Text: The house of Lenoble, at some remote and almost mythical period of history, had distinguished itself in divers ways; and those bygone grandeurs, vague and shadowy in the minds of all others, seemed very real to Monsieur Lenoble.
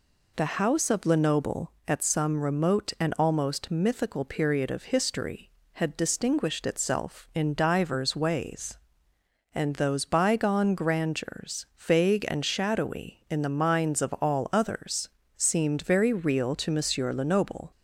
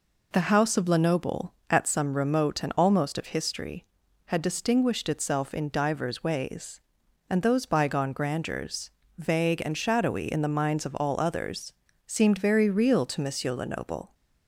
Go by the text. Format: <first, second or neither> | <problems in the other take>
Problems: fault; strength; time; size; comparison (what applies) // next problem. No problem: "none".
first | skips "mythical period"; at 3.1 s